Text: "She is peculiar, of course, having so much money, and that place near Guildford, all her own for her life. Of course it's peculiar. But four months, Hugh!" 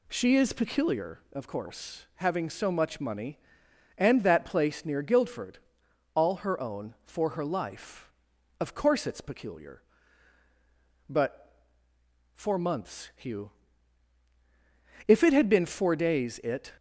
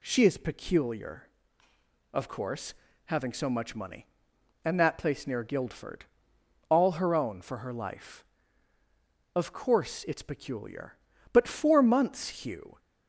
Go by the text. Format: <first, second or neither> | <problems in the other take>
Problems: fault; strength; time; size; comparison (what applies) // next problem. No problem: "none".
second | pauses between "But" and "four"; noticeable; at 11.6 s; 0.72 s long // goes on to say "If it had been four days it"; strong; from 15.0 s on; 1.6 s long